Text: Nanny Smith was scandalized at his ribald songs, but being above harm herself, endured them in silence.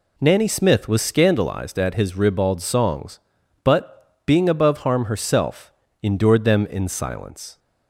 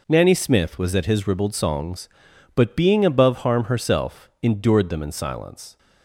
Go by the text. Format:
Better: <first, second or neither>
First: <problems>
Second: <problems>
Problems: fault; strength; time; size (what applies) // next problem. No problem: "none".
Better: first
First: none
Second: skips "scandalized"; at 0.9 s